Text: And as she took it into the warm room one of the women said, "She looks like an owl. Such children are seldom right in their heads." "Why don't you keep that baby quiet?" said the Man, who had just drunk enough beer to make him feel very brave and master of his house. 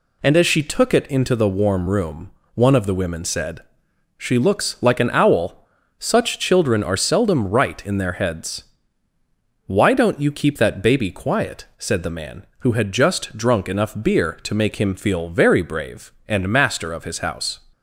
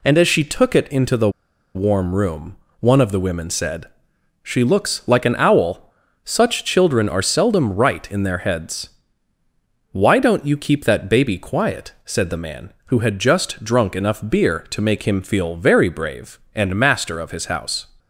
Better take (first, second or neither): first